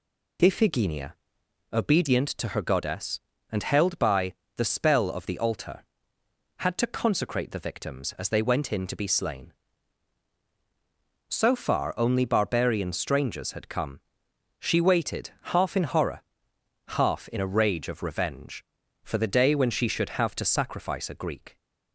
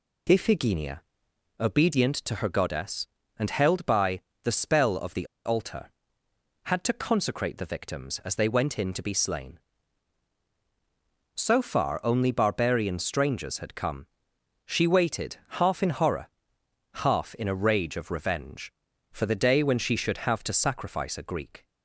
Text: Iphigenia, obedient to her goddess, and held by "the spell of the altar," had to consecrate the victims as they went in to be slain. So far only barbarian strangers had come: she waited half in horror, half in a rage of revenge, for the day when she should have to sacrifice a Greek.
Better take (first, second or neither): first